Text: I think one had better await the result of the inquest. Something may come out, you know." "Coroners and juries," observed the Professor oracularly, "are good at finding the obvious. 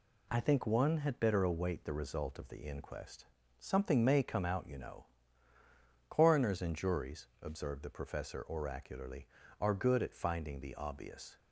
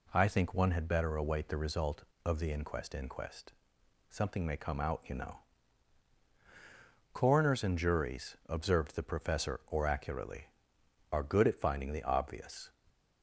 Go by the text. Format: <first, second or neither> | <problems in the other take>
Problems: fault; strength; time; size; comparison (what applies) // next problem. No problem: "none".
first | says "inquest" twice; at 2.9 s // stays silent after the last word; slight; from 12.6 s on; 0.6 s long